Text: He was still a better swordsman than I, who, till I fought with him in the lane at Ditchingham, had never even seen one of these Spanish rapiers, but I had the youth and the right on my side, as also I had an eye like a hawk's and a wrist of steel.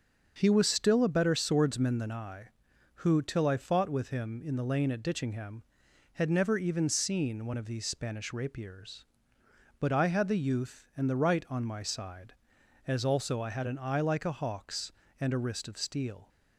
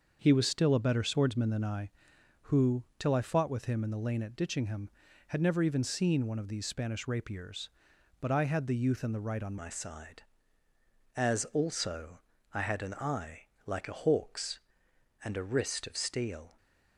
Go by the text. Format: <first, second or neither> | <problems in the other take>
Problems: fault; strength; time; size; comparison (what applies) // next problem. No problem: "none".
first | starts louder than the rest; until 1.2 s; 6.5 dB; also in the first // changes voice at "my"; from 9.5 s on; 7.0 s long // pauses between "also" and "I"; slight; at 12.2 s; 0.34 s long // pauses between "eye" and "like"; slight; at 13.4 s; 0.18 s long